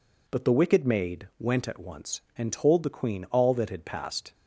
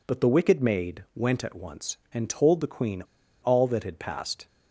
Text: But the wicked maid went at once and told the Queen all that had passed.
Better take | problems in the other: first | pauses between "Queen" and "all"; at 3.0 s; 0.38 s long

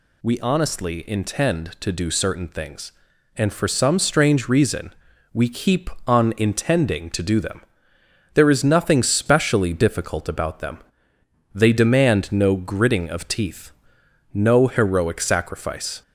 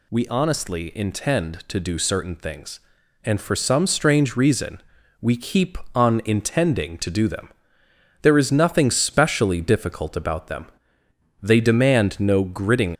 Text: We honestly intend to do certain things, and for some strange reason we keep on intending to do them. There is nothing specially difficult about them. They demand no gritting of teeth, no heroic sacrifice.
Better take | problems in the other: first | pauses between "reason" and "we"; at 4.8 s; 0.40 s long; also in the first // stops before "of teeth no heroic sacrifice"; at 12.9 s

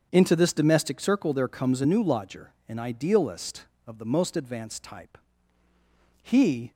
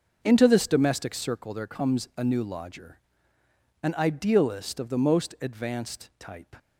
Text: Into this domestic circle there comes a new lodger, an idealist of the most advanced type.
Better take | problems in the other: second | starts louder than the rest; strong; until 1.1 s; 7 dB; noticeable in the second // goes on to say "He"; from 6.2 s on; 0.50 s long

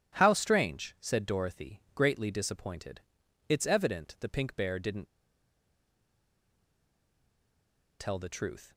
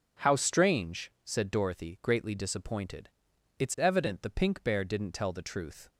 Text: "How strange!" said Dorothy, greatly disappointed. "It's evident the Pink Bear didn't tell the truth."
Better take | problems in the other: second | pauses between "didn't" and "tell"; strong; at 5.0 s; 2.9 s long

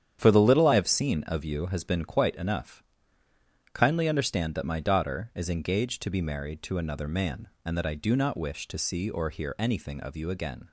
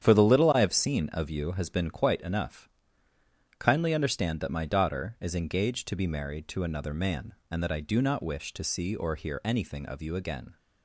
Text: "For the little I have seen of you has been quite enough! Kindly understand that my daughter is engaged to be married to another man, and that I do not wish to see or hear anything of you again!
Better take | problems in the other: neither | starts louder than the rest; strong; the same in both

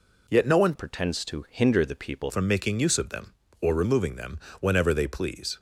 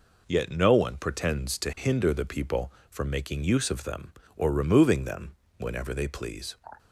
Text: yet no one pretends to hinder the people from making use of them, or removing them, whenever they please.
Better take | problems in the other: second | changes voice from "pretends" to "people"; from 0.7 to 2.3 s; 1.6 s long

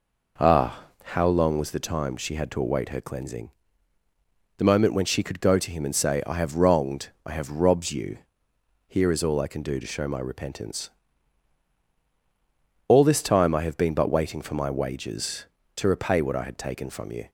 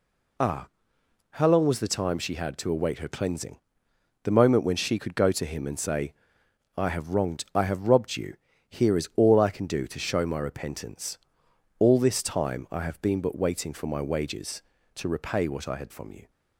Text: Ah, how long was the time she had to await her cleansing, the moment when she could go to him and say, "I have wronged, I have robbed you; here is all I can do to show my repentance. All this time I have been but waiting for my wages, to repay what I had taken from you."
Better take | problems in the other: first | skips "taken"; at 15.9 s

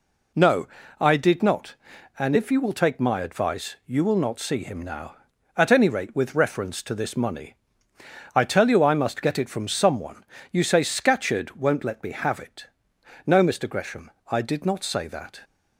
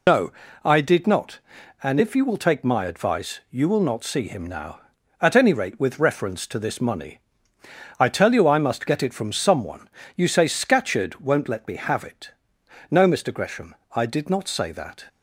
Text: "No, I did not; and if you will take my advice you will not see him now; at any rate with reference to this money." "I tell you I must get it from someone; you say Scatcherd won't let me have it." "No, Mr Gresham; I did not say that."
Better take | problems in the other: first | loses the start of "No"; at 0.0 s; 80 ms

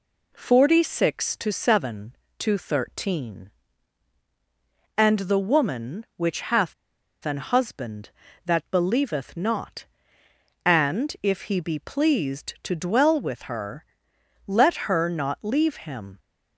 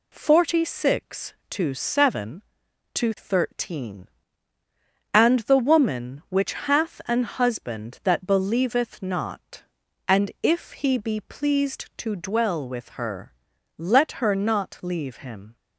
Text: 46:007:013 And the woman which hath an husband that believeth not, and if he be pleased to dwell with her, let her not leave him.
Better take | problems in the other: second | pauses between "hath" and "an"; noticeable; at 6.7 s; 0.52 s long

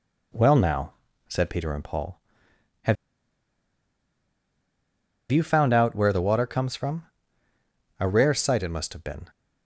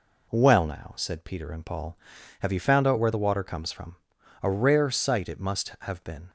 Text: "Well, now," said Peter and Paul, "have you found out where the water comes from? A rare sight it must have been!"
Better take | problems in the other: second | pauses between "have" and "you"; strong; at 2.9 s; 2.3 s long

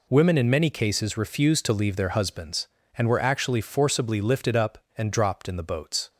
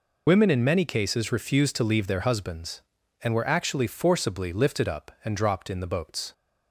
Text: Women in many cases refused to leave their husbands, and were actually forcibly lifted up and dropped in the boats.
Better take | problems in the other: first | loses the start of "Women"; at 0.2 s; 65 ms

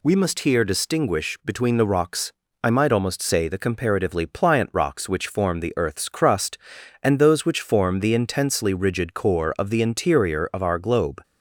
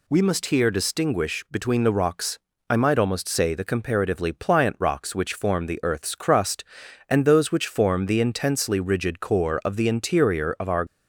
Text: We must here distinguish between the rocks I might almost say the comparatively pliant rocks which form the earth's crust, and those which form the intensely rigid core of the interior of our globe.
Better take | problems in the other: first | pauses between "rocks" and "I"; slight; at 2.3 s; 0.30 s long; slight in the first // stops before "globe"; at 10.8 s

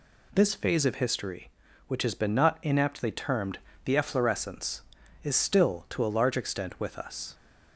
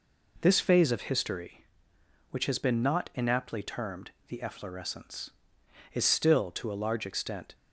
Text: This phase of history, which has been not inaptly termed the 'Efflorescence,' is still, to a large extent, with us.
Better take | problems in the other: first | pauses between "termed" and "the"; slight; at 4.1 s; 0.16 s long; slight in the first // stops before "with us"; at 7.5 s

